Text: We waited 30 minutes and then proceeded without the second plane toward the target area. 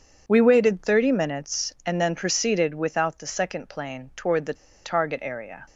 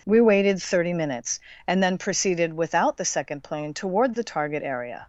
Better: second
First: pauses between "the" and "target"; slight; at 4.5 s; 0.30 s long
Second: none

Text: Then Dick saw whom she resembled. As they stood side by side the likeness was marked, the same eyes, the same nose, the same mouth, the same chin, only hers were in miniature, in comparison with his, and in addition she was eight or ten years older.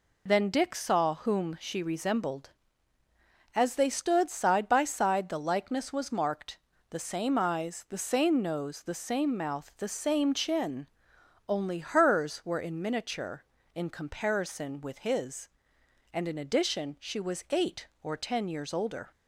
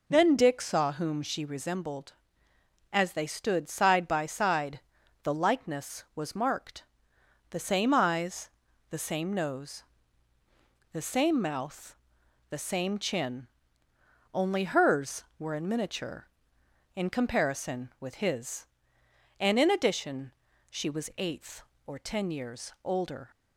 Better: first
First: none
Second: pauses between "side" and "the"; at 4.8 s; 0.44 s long // pauses between "addition" and "she"; at 20.3 s; 0.40 s long // says "eighth" for "eight"; at 21.1 s

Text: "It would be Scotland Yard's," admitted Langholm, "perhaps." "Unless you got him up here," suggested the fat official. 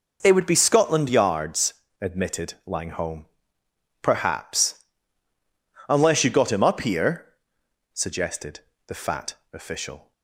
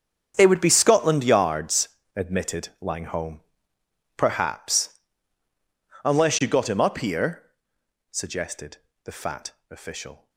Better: first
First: pauses between "suggested" and "the"; slight; at 8.5 s; 0.28 s long // pauses between "fat" and "official"; slight; at 9.3 s; 0.18 s long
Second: gets quieter; strong; throughout; 16.5 dB // pauses between "suggested" and "the"; slight; at 8.7 s; 0.28 s long // pauses between "fat" and "official"; slight; at 9.5 s; 0.18 s long

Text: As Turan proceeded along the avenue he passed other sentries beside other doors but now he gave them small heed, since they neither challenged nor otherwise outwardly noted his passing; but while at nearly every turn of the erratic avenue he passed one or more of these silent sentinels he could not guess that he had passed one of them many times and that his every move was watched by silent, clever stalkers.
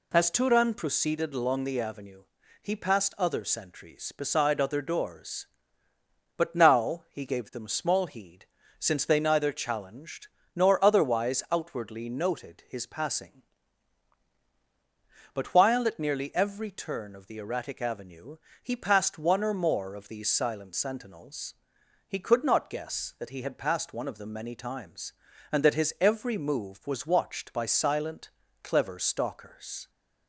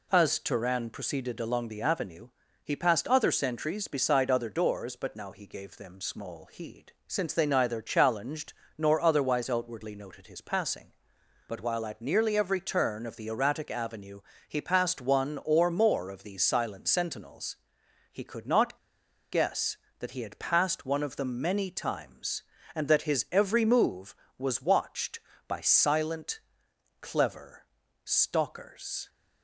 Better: first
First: pauses between "avenue" and "he"; slight; at 2.2 s; 0.36 s long // pauses between "challenged" and "nor"; slight; at 10.2 s; 0.28 s long // pauses between "avenue" and "he"; slight; at 18.3 s; 0.26 s long // pauses between "sentinels" and "he"; noticeable; at 21.5 s; 0.52 s long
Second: pauses between "avenue" and "he"; slight; at 2.2 s; 0.36 s long // pauses between "challenged" and "nor"; slight; at 8.5 s; 0.24 s long // pauses between "avenue" and "he"; slight; at 14.2 s; 0.26 s long // pauses between "sentinels" and "he"; noticeable; at 17.5 s; 0.54 s long // pauses between "not" and "guess"; noticeable; at 18.7 s; 0.54 s long // pauses between "clever" and "stalkers"; at 27.6 s; 0.40 s long

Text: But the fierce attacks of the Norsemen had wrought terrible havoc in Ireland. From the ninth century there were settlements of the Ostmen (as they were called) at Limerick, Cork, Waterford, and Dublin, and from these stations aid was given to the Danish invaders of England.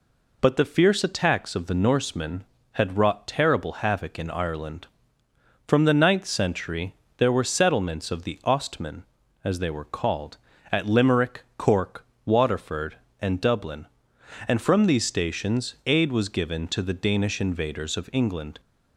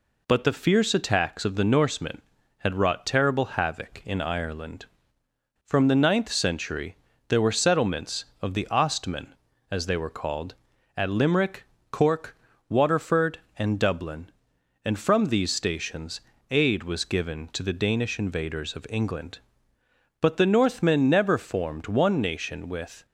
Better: first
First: pauses between "century" and "there"; slight; at 6.9 s; 0.24 s long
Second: pauses between "century" and "there"; slight; at 6.9 s; 0.34 s long // pauses between "stations" and "aid"; slight; at 16.1 s; 0.32 s long // goes on to say "But the Northmen never formed one nation with"; strong; from 20.1 s on; 2.8 s long

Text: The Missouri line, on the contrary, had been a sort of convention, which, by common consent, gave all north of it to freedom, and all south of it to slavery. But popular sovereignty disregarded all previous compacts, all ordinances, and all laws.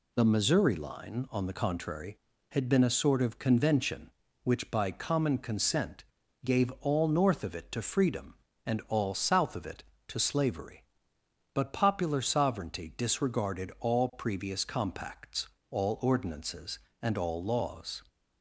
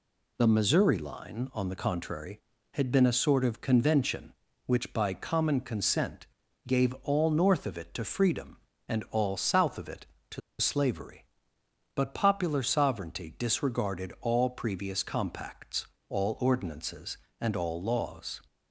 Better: first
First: none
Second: pauses between "to" and "slavery"; slight; at 10.4 s; 0.19 s long

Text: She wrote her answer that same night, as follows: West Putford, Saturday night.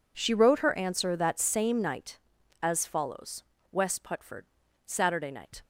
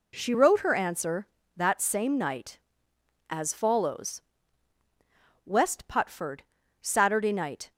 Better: neither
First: none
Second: none

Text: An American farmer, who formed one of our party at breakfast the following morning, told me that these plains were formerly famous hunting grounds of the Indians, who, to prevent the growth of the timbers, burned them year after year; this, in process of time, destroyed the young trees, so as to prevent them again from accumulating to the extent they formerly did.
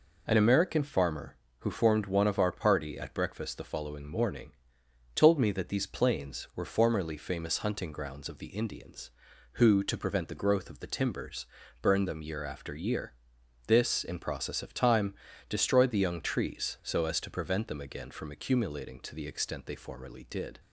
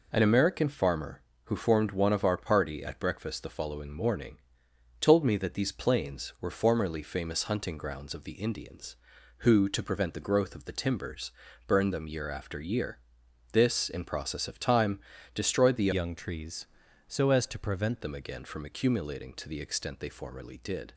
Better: first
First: none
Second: changes voice from "young" to "prevent"; from 15.9 to 18.0 s; 2.1 s long

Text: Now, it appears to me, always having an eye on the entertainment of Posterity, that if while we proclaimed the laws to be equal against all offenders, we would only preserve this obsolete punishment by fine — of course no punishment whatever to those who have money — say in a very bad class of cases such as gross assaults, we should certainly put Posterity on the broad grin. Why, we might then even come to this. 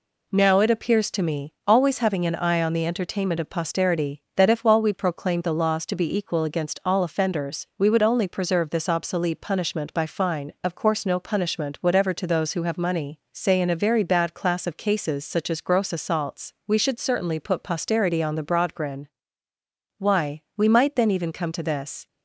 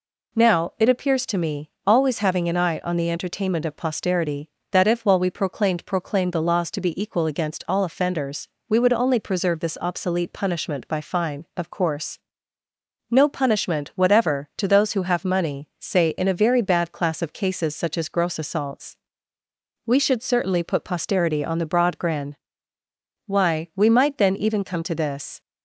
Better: first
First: none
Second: says "proclaimed" twice; at 5.8 s // pauses between "course" and "no"; noticeable; at 12.1 s; 0.94 s long

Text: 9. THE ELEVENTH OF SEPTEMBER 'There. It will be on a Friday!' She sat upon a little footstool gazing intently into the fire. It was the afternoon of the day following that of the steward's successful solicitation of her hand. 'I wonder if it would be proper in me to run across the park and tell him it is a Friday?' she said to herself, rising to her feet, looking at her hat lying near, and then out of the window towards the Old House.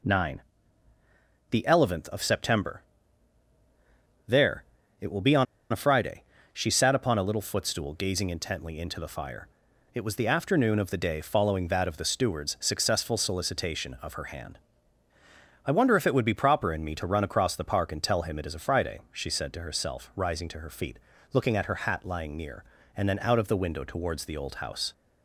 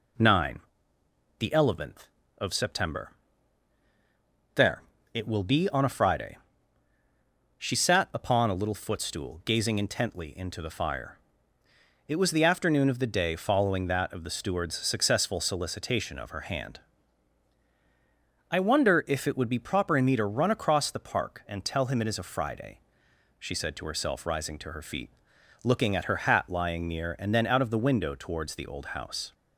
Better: second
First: pauses between "SEPTEMBER" and "There"; strong; at 2.8 s; 1.4 s long // pauses between "on" and "a"; slight; at 5.4 s; 0.27 s long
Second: pauses between "SEPTEMBER" and "There"; strong; at 3.1 s; 1.4 s long

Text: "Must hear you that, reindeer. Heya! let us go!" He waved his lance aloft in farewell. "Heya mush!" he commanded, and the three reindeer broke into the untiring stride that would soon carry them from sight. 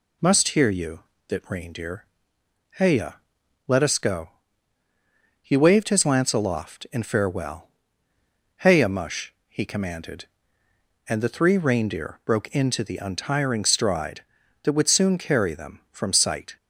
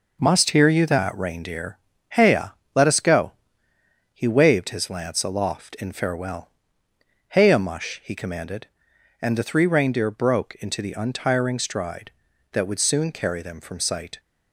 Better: neither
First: none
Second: none

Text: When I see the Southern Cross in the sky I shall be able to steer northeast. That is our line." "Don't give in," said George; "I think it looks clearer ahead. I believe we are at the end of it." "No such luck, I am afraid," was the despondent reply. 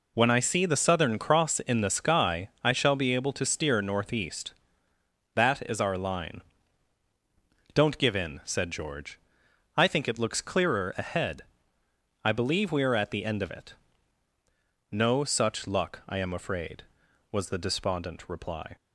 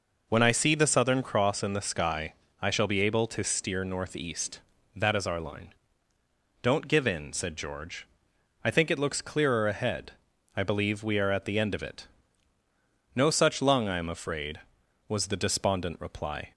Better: first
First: none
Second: pauses between "sky" and "I"; slight; at 2.3 s; 0.26 s long // says "lung" for "luck"; at 13.6 s

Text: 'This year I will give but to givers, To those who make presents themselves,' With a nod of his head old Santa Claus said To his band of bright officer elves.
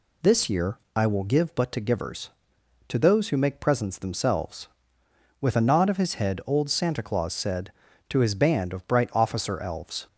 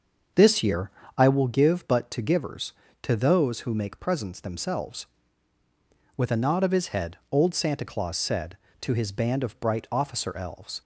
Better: first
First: pauses between "year" and "I"; slight; at 0.7 s; 0.18 s long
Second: starts louder than the rest; until 1.4 s; 6.5 dB // pauses between "year" and "I"; slight; at 0.9 s; 0.26 s long

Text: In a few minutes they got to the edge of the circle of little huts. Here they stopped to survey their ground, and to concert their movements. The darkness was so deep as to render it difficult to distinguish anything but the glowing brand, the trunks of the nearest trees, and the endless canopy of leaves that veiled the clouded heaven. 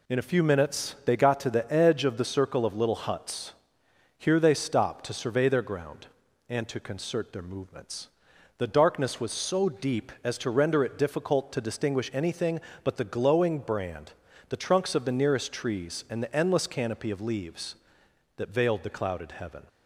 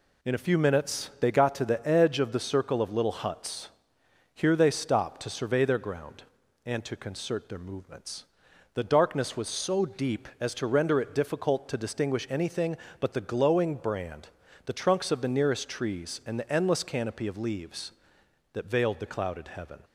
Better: neither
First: none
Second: none

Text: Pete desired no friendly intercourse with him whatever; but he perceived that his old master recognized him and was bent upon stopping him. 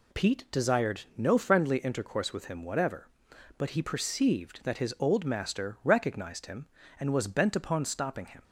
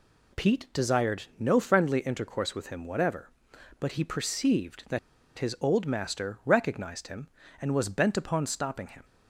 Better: first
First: none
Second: pauses between "that" and "his"; at 4.9 s; 0.39 s long

